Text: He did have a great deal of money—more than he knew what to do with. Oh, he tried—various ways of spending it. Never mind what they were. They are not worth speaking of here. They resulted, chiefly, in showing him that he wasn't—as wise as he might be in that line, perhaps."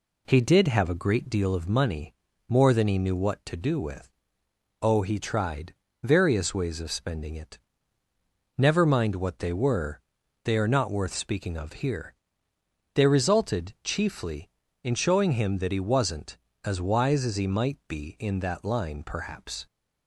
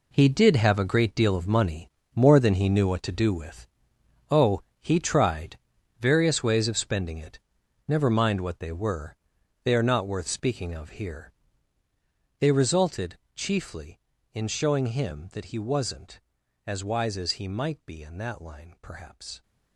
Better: first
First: none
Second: gets quieter; strong; throughout; 11.5 dB

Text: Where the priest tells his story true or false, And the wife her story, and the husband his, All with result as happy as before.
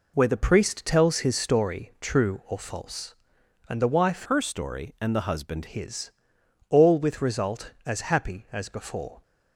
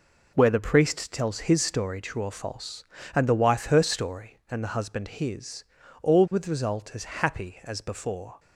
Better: second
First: changes voice from "her" to "husband"; from 4.2 to 5.6 s; 1.4 s long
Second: none

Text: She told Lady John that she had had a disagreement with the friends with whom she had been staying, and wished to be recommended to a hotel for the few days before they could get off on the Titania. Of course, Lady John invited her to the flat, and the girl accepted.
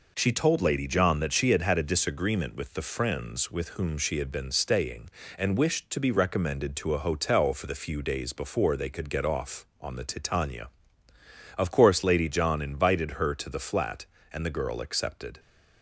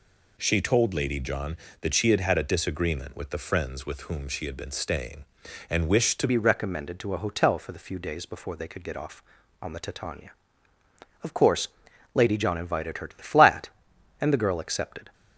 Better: first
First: none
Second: changes voice at "be"; from 6.2 s on; 8.9 s long

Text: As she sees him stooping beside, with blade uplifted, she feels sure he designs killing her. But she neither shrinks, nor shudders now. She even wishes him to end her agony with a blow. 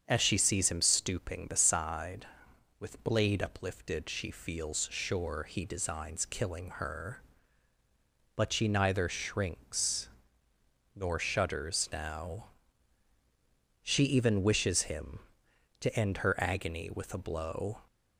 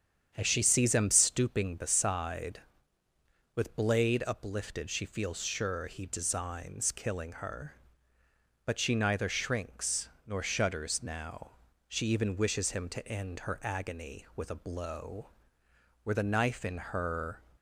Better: first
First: starts louder than the rest; strong; until 1.0 s; 7.5 dB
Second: starts louder than the rest; strong; until 1.3 s; 8 dB // goes on to say "Were the knife in her"; from 16.0 s on; 1.3 s long

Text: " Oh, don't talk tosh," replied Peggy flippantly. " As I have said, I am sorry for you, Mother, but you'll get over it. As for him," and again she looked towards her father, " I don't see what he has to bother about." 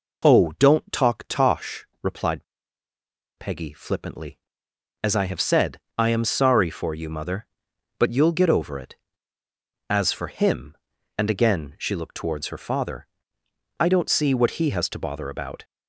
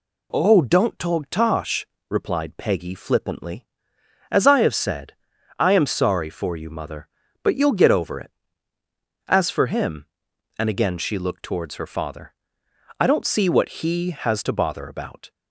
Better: second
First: pauses between "replied" and "Peggy"; noticeable; at 2.4 s; 0.93 s long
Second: none

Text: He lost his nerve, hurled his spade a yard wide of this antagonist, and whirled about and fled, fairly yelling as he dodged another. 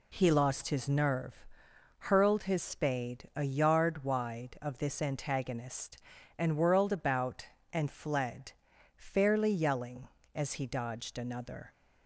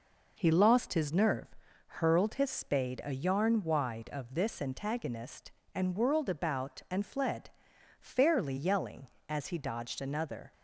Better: first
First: none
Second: says "yarn" for "yard"; at 3.1 s

